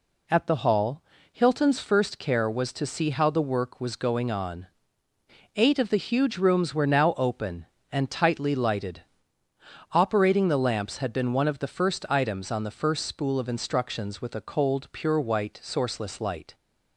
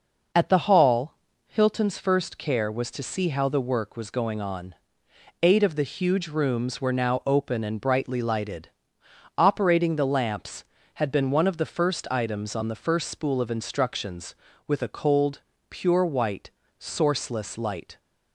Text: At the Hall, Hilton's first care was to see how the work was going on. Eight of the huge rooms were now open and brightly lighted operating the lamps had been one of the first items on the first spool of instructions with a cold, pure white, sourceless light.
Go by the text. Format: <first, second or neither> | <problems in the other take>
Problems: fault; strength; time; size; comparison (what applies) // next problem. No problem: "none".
second | says "tightly" for "brightly"; at 8.1 s // pauses between "lighted" and "operating"; noticeable; at 9.0 s; 0.90 s long; noticeable in the second